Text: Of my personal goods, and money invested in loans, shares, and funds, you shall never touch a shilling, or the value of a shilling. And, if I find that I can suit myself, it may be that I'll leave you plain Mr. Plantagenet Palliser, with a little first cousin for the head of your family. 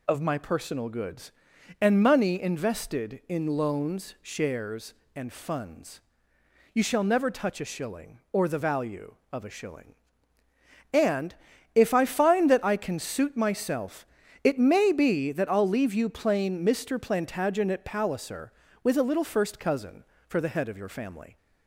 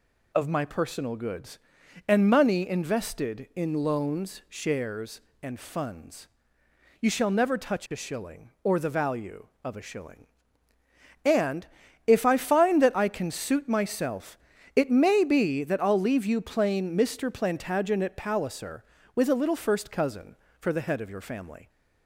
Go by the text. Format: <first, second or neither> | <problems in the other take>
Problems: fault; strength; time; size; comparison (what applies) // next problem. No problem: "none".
neither | none